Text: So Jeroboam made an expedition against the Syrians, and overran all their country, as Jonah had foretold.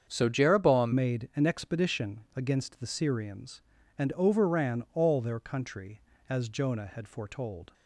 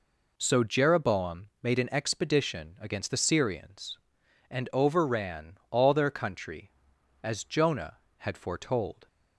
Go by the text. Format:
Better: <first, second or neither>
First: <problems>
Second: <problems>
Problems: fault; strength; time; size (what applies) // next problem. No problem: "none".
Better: second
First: starts louder than the rest; strong; until 1.1 s; 7.5 dB // changes voice at "made"; from 0.9 s on; 6.8 s long // pauses between "expedition" and "against"; slight; at 2.2 s; 0.16 s long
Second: none